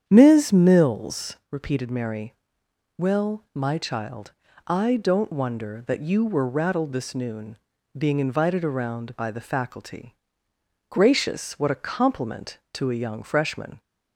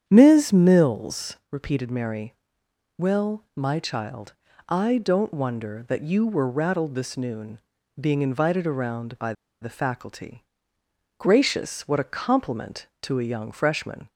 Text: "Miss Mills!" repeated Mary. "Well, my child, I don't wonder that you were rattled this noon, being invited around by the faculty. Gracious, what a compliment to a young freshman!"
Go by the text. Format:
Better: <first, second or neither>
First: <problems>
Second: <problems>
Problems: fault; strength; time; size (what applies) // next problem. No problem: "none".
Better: first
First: starts louder than the rest; strong; until 1.0 s; 8.5 dB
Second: starts louder than the rest; strong; until 1.0 s; 8.5 dB // pauses between "by" and "the"; slight; at 9.3 s; 0.29 s long